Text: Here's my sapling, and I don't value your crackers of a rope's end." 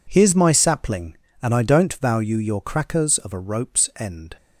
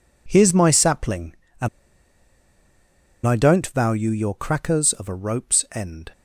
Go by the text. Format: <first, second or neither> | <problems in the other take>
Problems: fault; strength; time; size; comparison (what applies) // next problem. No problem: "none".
first | pauses between "and" and "I"; strong; at 1.6 s; 1.5 s long